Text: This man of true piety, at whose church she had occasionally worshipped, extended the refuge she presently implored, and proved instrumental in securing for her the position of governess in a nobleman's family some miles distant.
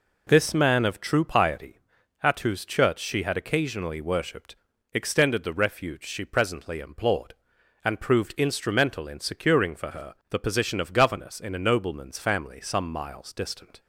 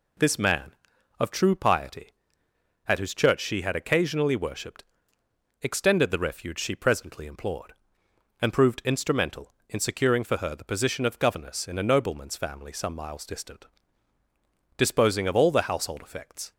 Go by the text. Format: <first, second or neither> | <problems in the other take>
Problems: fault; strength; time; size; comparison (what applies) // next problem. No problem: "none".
first | goes on to say "Disposing of all the household effects"; strong; from 14.7 s on; 1.7 s long